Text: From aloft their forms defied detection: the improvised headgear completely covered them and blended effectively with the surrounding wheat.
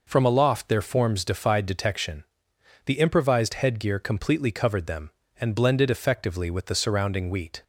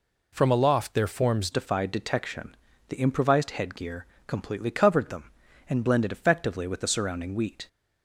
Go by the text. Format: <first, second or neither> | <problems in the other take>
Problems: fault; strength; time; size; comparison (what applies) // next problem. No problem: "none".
first | changes voice at "defied"; from 1.5 s on; 6.1 s long // pauses between "headgear" and "completely"; slight; at 4.0 s; 0.22 s long